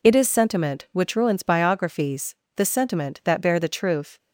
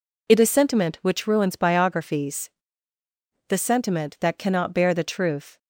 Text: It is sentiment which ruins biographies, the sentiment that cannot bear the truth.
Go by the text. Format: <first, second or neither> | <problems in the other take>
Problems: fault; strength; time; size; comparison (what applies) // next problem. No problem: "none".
second | skips "cannot"; at 3.4 s